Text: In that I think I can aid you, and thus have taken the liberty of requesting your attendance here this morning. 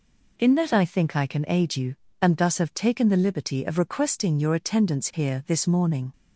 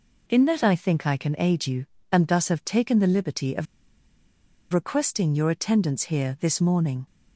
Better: first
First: none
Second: pauses between "of" and "requesting"; at 3.6 s; 1.0 s long

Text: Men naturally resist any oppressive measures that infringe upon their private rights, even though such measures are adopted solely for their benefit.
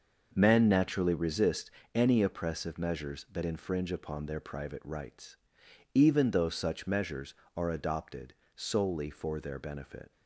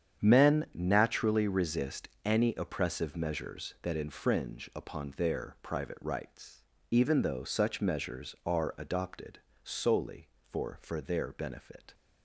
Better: first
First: pauses between "resist" and "any"; slight; at 1.7 s; 0.24 s long // pauses between "adopted" and "solely"; slight; at 8.3 s; 0.24 s long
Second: starts louder than the rest; strong; until 1.2 s; 8.5 dB // pauses between "resist" and "any"; slight; at 2.0 s; 0.16 s long // pauses between "adopted" and "solely"; slight; at 9.3 s; 0.26 s long // says "for" twice; at 10.8 s

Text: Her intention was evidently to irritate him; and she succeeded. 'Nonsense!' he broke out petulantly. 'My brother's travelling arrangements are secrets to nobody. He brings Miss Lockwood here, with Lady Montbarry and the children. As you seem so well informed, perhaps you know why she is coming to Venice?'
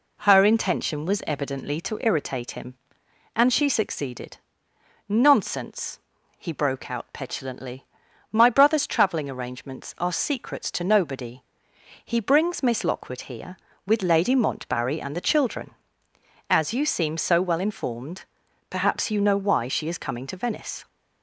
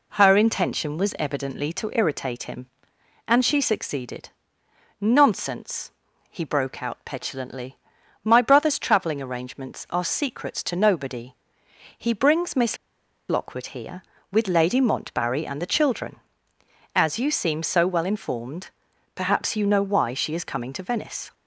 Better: first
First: none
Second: pauses between "Miss" and "Lockwood"; noticeable; at 12.7 s; 0.52 s long

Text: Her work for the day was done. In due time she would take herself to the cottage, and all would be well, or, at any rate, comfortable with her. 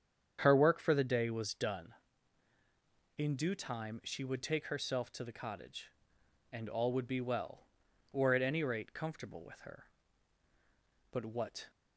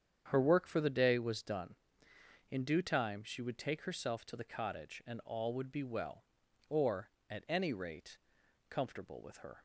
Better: second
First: starts louder than the rest; strong; until 1.4 s; 8 dB // goes on to say "But what"; from 11.0 s on; 0.60 s long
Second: starts louder than the rest; strong; until 1.3 s; 8 dB

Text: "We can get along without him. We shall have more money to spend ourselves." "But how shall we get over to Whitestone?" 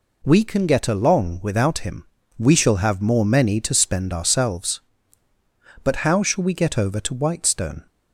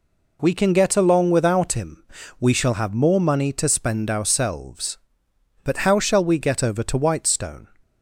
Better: second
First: says "many" for "money"; at 3.2 s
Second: none

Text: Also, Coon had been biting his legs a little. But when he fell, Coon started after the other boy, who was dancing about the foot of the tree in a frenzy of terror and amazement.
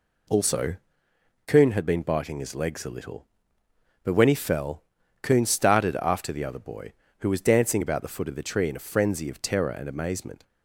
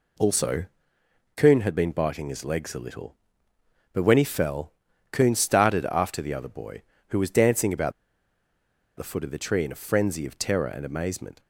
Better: first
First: none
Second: pauses between "about" and "the"; at 7.9 s; 1.0 s long

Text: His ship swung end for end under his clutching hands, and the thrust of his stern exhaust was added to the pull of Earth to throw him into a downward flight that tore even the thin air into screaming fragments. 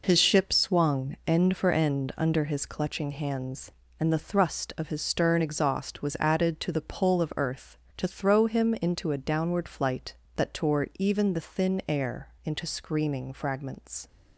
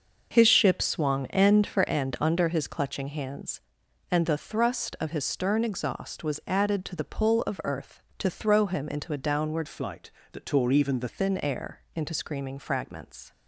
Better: first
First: none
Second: starts louder than the rest; noticeable; until 1.3 s; 6 dB // changes voice from "flight" to "the"; from 9.6 to 11.0 s; 1.4 s long

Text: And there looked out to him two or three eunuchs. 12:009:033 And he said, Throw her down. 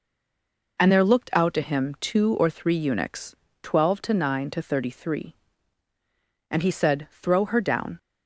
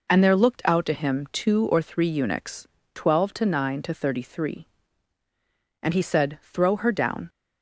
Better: second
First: stays silent before the first word; slight; until 0.7 s; 0.7 s long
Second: none

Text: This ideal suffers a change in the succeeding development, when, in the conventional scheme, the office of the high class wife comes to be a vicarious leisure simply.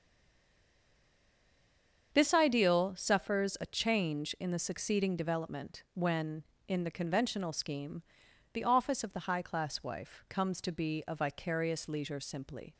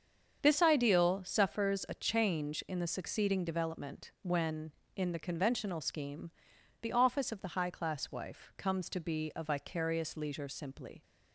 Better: second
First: stays silent before the first word; until 2.1 s; 2.1 s long // starts louder than the rest; strong; until 3.1 s; 7.5 dB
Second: starts louder than the rest; strong; until 1.4 s; 7.5 dB

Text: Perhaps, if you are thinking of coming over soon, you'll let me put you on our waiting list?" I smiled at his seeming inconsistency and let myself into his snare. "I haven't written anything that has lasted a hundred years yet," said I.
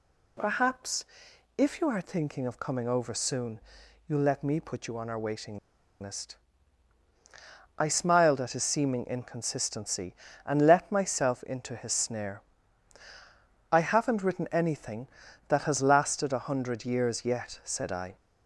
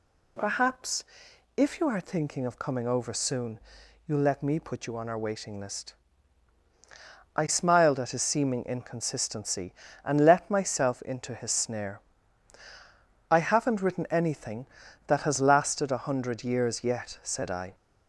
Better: second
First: pauses between "waiting" and "list"; at 5.5 s; 0.42 s long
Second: none

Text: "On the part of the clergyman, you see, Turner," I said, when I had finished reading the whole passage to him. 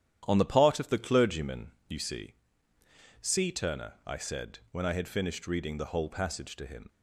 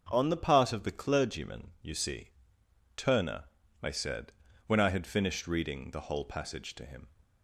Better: second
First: starts louder than the rest; strong; until 1.2 s; 10.5 dB // says "see" twice; at 3.1 s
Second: starts louder than the rest; until 1.1 s; 6.5 dB

